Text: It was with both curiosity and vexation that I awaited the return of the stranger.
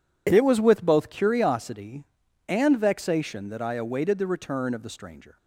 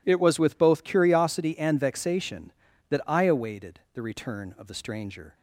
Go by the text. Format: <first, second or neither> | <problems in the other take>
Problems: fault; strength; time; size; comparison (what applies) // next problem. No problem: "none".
neither | none